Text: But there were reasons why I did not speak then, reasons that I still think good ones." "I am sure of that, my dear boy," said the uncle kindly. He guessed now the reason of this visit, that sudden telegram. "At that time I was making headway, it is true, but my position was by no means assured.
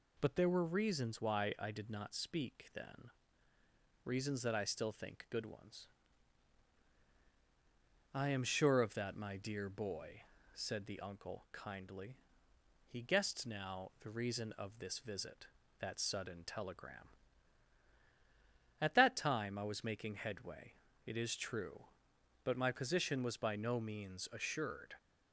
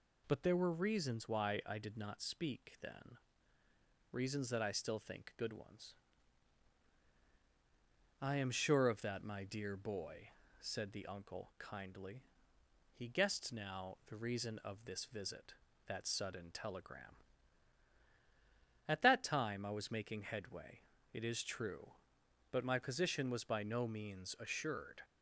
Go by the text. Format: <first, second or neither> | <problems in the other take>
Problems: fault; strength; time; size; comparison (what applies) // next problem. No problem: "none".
neither | none